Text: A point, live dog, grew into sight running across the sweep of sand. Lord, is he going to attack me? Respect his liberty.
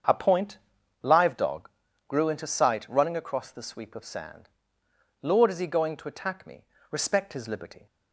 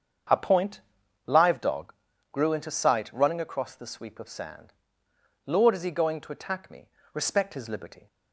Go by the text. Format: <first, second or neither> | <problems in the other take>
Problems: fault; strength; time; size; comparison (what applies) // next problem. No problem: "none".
neither | starts louder than the rest; strong; the same in both